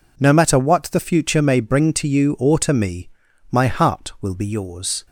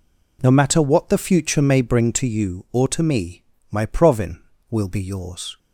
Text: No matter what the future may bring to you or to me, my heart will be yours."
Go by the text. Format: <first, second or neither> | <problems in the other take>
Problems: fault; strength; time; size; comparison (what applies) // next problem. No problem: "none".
first | says "provin" for "heart"; at 3.8 s